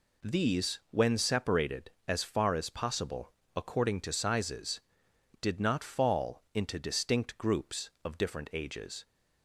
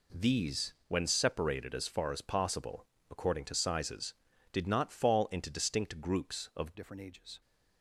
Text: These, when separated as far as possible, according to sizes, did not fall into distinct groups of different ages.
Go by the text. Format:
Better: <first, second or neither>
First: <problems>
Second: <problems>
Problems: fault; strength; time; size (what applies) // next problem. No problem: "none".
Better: first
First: none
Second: changes voice at "different"; from 6.7 s on; 0.7 s long